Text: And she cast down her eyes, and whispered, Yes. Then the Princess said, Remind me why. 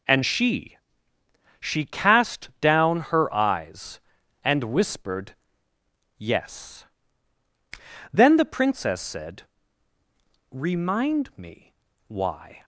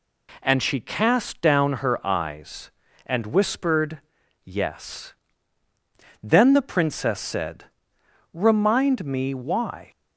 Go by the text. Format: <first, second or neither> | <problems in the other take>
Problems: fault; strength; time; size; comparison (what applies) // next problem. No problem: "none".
second | says "she" twice; at 1.6 s // pauses between "me" and "why"; slight; at 11.7 s; 0.34 s long